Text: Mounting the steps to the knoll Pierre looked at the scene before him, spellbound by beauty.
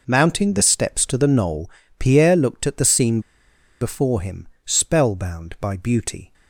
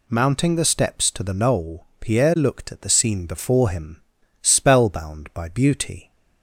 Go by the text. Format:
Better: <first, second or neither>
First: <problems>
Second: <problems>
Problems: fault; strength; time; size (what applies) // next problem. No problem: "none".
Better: second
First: pauses between "knoll" and "Pierre"; slight; at 1.7 s; 0.28 s long // pauses between "scene" and "before"; noticeable; at 3.2 s; 0.60 s long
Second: none